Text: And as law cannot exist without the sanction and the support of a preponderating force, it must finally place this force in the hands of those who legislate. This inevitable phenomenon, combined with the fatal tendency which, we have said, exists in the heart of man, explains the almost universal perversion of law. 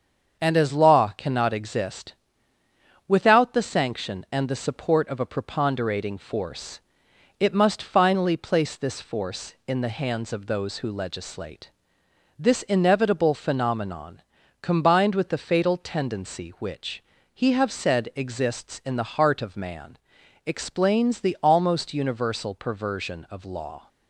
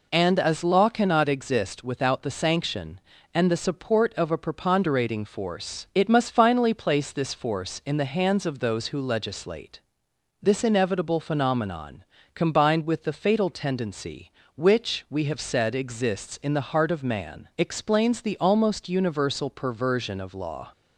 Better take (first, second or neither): second